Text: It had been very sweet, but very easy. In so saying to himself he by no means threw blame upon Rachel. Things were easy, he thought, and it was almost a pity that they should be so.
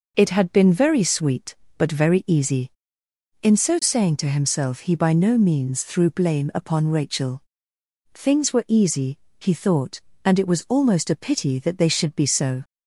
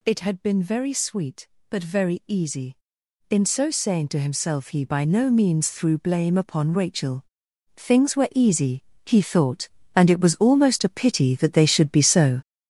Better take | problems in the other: first | gets louder; strong; throughout; 8 dB

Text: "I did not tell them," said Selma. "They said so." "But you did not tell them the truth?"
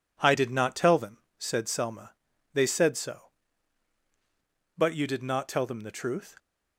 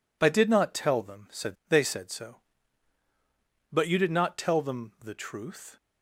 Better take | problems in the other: first | skips "Selma"; at 1.6 s

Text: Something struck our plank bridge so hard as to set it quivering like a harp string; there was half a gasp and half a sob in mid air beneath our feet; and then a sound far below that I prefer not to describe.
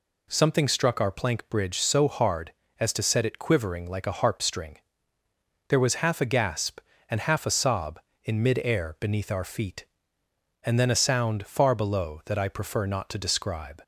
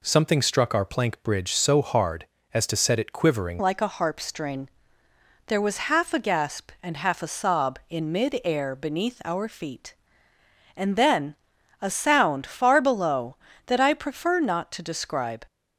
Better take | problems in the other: first | changes voice at "like"; from 3.5 s on; 11.9 s long // pauses between "then" and "a"; noticeable; at 11.3 s; 0.48 s long

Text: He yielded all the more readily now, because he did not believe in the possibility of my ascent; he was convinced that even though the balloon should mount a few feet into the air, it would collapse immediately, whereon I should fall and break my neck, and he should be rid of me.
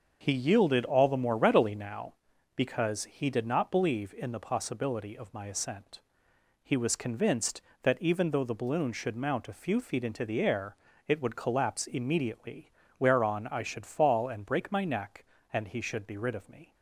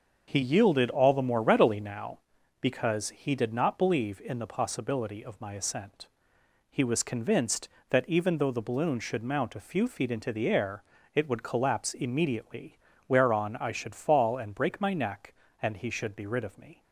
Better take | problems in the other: neither | starts louder than the rest; the same in both

